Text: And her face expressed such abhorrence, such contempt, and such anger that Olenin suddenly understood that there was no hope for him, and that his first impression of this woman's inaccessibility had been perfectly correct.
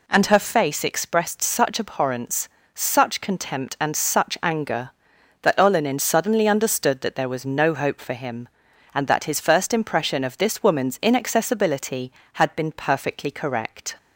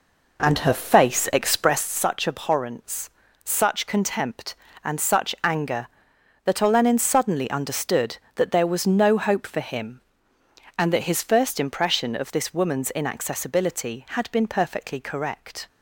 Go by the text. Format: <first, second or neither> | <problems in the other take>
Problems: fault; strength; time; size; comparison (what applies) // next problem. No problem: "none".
first | starts louder than the rest; noticeable; until 2.0 s; 4 dB